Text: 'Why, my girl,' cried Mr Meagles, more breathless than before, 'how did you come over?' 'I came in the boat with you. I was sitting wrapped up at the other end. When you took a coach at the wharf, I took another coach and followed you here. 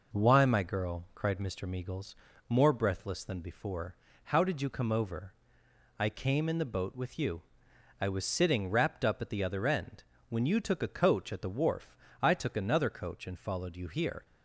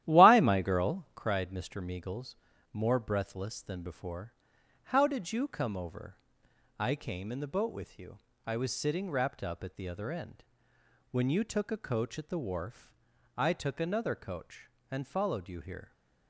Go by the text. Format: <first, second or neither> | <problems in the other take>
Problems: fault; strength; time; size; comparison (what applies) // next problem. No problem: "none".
first | starts louder than the rest; strong; until 1.3 s; 13 dB